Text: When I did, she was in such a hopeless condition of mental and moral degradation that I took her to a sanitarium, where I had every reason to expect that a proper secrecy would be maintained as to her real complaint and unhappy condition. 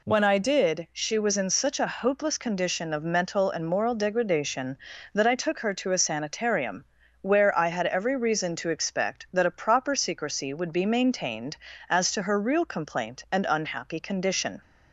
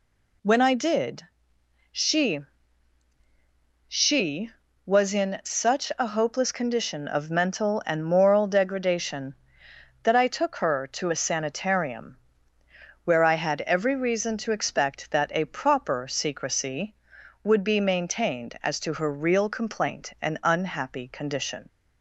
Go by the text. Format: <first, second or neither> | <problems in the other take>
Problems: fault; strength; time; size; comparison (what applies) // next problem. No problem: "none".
first | says "she" twice; at 3.8 s